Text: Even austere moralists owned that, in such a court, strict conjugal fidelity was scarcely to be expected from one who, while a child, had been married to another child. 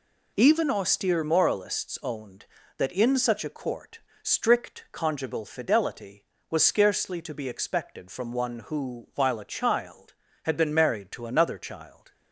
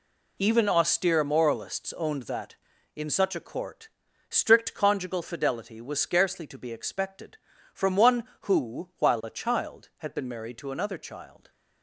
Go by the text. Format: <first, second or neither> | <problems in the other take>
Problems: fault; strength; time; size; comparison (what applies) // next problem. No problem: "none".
neither | none